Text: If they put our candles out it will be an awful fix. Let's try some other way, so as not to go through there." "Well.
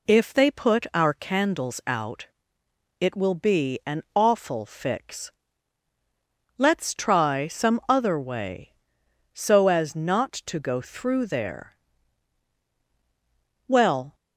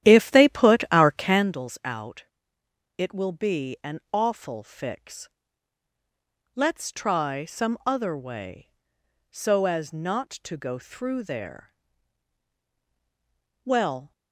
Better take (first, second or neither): first